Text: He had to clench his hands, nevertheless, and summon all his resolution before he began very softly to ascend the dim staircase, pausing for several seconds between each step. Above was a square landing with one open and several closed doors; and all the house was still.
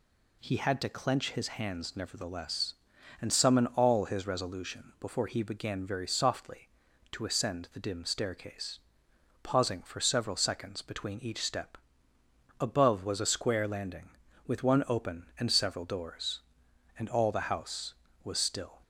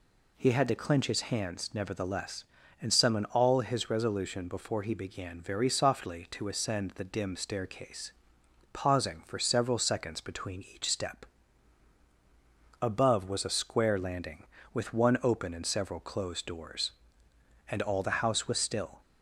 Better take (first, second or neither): second